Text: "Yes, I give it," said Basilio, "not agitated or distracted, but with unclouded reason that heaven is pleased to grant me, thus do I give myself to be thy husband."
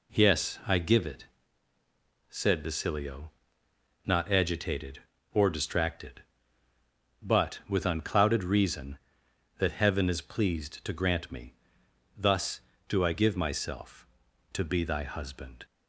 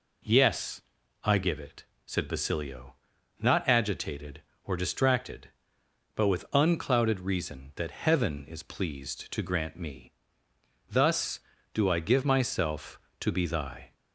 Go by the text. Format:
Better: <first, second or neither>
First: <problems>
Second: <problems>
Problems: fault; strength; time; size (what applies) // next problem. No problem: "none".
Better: first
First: none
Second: stops before "husband"; at 13.9 s